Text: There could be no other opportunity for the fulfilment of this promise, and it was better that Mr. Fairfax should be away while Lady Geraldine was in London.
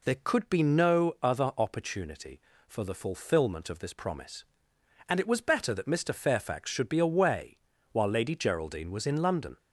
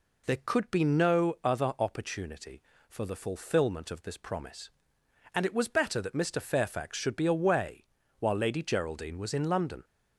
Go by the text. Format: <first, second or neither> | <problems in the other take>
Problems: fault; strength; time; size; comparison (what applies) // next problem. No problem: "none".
neither | pauses between "away" and "while"; slight; the same in both